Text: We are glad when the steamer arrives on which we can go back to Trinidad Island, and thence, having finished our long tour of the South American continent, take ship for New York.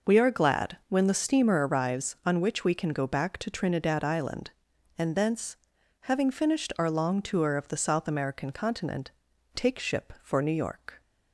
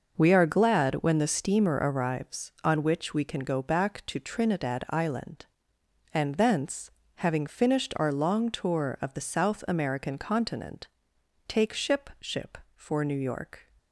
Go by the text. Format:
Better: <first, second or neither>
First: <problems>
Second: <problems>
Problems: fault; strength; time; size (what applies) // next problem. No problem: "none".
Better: first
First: none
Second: says "ship" twice; at 12.2 s